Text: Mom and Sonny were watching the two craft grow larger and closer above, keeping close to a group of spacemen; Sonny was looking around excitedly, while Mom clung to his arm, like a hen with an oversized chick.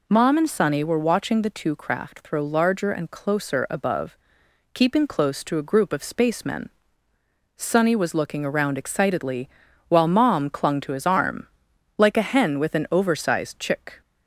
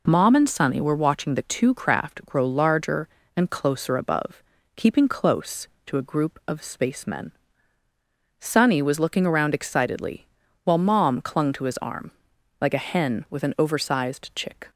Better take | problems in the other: second | says "throw" for "grow"; at 2.1 s

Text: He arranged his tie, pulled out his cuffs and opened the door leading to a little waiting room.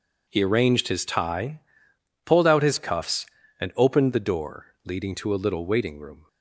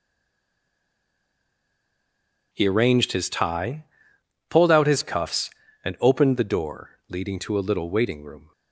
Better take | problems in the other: first | stays silent before the first word; strong; until 2.5 s; 2.5 s long // pauses between "door" and "leading"; slight; at 6.8 s; 0.20 s long; slight in the first

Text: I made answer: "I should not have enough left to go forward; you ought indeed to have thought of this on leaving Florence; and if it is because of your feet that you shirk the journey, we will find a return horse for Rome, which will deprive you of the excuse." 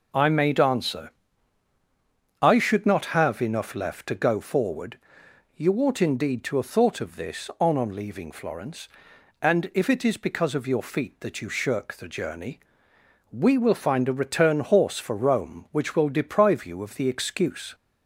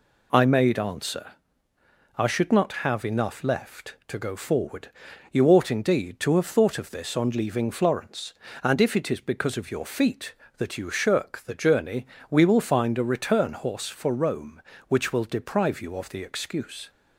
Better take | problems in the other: second | says "on" twice; at 7.7 s

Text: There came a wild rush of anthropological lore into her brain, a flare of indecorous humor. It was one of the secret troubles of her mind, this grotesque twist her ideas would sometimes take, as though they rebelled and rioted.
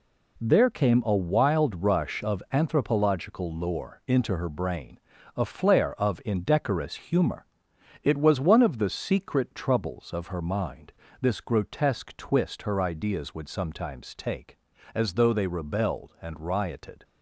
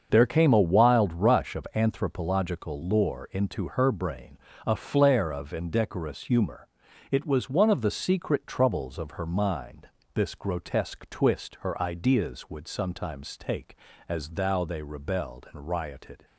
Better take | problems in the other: first | starts louder than the rest; until 1.1 s; 6.5 dB // says "thou" for "though"; at 14.2 s

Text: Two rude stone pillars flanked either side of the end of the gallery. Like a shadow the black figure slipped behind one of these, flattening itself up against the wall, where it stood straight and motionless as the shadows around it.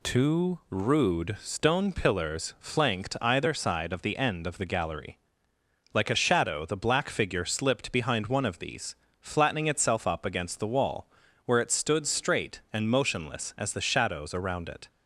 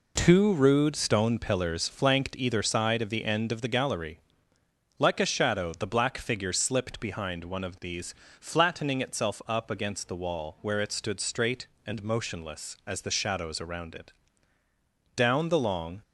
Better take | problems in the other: first | goes on to say "Down the long"; noticeable; from 15.1 s on; 0.86 s long

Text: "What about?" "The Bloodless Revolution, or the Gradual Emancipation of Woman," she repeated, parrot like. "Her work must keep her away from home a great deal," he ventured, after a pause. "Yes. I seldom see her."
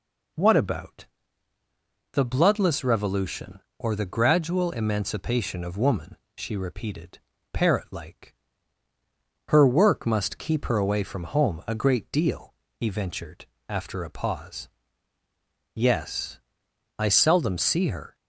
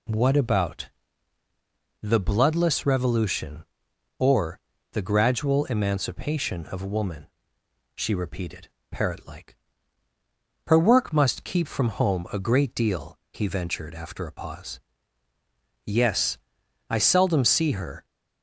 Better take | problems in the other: first | pauses between "or" and "the"; slight; at 4.5 s; 0.34 s long // skips "her away"; at 11.6 s

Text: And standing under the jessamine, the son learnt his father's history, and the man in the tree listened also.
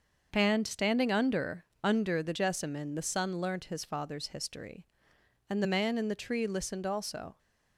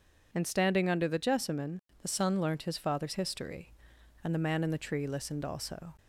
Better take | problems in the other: second | starts louder than the rest; until 1.3 s; 6.5 dB // says "under" twice; at 1.8 s

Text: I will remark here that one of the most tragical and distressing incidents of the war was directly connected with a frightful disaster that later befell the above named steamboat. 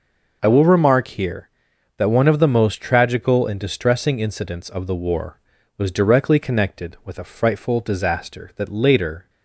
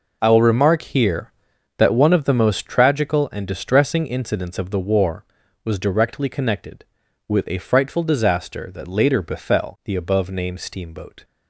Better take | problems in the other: second | stops before "befell the above named steamboat"; at 9.2 s

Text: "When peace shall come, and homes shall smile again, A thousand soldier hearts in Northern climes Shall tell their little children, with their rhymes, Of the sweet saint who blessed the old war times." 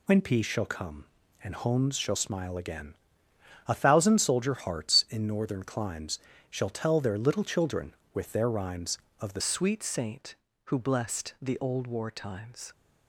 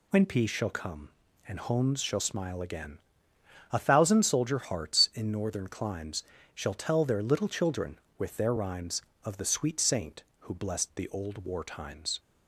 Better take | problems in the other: second | pauses between "climes" and "Shall"; slight; at 6.1 s; 0.32 s long; slight in the second // changes voice at "sweet"; from 9.4 s on; 3.3 s long

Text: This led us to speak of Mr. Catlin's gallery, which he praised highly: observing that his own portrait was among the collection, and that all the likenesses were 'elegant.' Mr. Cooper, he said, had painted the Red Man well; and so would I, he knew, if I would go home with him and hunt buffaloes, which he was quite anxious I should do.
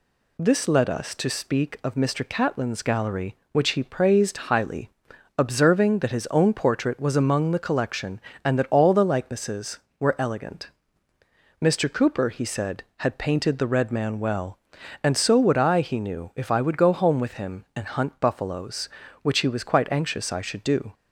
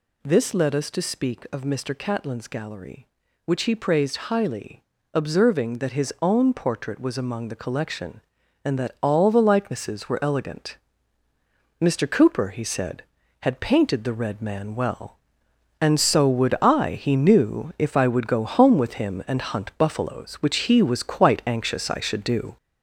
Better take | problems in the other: first | gets louder; noticeable; throughout; 5.5 dB

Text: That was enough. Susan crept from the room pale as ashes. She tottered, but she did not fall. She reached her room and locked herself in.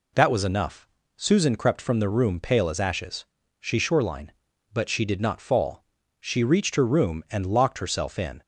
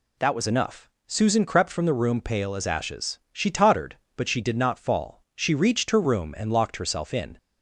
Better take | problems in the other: second | says "shoreline" for "tottered"; at 3.7 s

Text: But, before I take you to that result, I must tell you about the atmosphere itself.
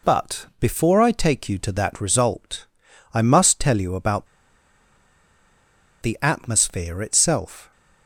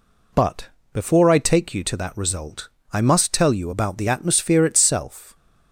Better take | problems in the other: second | pauses between "about" and "the"; strong; at 4.2 s; 1.7 s long

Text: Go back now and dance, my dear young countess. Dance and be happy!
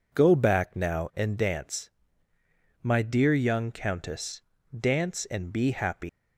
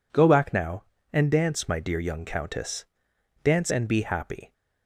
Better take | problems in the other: second | leaves "happy" unfinished; at 6.0 s; 145 ms

